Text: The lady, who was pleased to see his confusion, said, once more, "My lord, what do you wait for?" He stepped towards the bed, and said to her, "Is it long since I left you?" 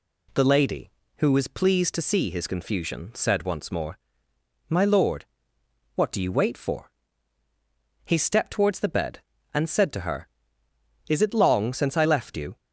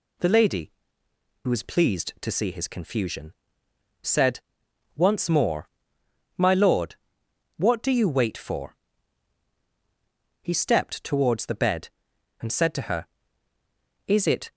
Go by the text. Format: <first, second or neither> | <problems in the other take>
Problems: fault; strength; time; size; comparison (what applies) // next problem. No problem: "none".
first | stops before "long since I left you"; at 14.5 s